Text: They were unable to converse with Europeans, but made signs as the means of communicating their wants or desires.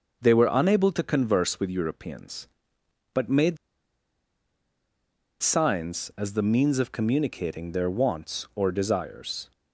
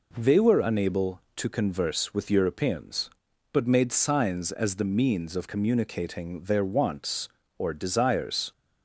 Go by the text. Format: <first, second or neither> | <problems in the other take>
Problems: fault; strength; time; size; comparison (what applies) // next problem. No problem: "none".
second | starts louder than the rest; until 1.2 s; 6.5 dB // pauses between "made" and "signs"; strong; at 3.5 s; 1.8 s long